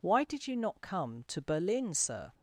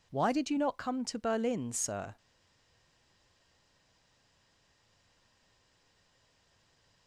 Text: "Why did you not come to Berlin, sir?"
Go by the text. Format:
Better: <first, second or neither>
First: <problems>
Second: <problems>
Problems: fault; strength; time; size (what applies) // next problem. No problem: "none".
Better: first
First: none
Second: stays silent after the last word; strong; from 2.1 s on; 4.9 s long